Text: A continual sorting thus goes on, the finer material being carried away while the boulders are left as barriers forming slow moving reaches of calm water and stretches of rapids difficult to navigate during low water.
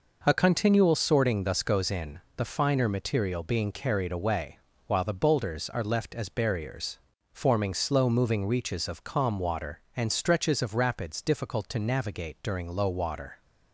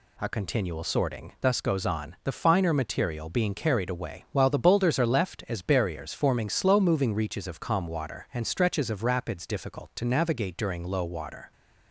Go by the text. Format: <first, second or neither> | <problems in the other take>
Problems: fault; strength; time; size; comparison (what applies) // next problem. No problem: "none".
second | says "in" for "on"; at 1.8 s // pauses between "away" and "while"; slight; at 4.5 s; 0.26 s long // pauses between "barriers" and "forming"; slight; at 6.9 s; 0.32 s long